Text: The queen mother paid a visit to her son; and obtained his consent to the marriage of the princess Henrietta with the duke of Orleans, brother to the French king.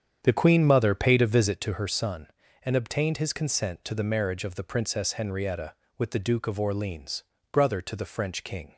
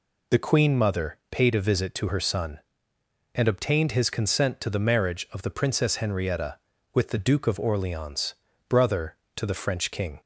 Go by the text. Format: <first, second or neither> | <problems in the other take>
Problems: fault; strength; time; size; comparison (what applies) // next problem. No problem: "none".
second | starts louder than the rest; strong; until 1.6 s; 8.5 dB